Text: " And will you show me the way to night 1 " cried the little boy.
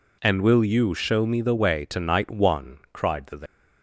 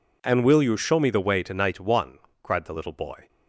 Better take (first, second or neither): second